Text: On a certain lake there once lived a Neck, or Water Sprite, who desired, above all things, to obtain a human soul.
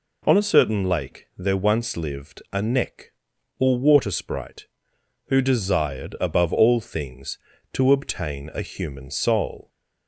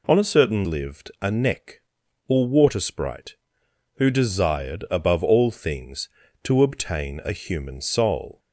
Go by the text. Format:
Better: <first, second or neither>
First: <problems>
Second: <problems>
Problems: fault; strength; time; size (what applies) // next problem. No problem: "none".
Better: first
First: none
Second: skips "lake there once"; at 0.6 s